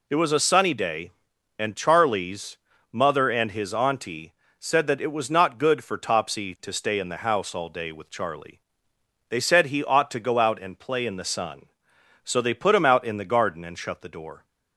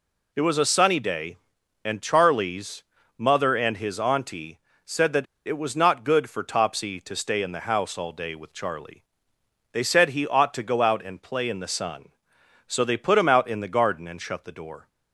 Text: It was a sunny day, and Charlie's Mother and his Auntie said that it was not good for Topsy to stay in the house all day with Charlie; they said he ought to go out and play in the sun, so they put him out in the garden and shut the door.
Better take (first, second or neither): first